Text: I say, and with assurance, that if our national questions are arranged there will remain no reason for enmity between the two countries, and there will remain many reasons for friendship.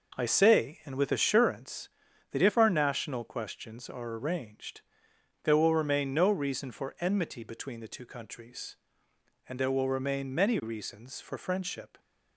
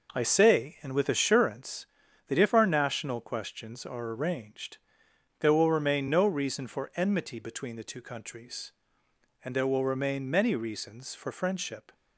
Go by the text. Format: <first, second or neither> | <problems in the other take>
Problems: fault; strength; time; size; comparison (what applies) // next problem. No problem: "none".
neither | pauses between "arranged" and "there"; noticeable; the same in both